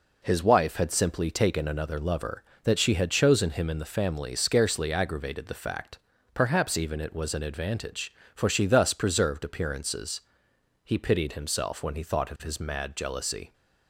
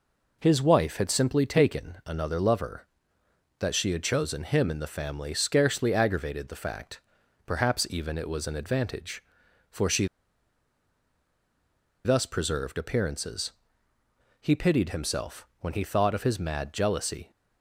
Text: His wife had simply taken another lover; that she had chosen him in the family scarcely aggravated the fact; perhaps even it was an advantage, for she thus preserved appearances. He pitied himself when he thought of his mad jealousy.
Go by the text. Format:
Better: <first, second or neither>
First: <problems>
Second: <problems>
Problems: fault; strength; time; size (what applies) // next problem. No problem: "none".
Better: first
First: none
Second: pauses between "she" and "thus"; strong; at 10.0 s; 1.9 s long